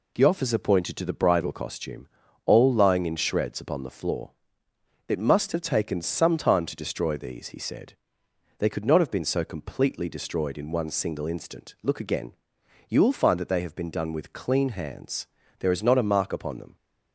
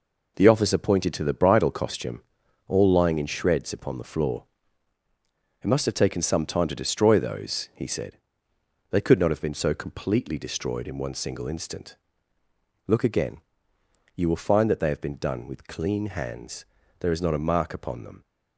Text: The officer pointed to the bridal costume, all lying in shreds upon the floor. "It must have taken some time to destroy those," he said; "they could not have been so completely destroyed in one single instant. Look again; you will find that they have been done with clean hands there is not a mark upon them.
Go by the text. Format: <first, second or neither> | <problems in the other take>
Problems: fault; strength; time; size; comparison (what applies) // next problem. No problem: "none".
second | says "these" for "those"; at 7.1 s // pauses between "hands" and "there"; slight; at 15.2 s; 0.32 s long; slight in the second